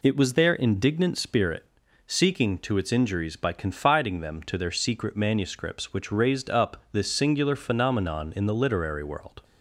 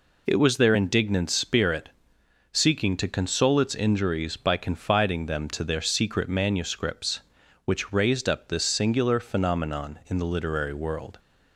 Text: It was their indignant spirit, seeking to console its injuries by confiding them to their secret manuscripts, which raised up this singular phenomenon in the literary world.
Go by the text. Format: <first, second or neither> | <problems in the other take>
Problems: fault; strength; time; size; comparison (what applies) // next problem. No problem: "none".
second | skips "console"; at 2.7 s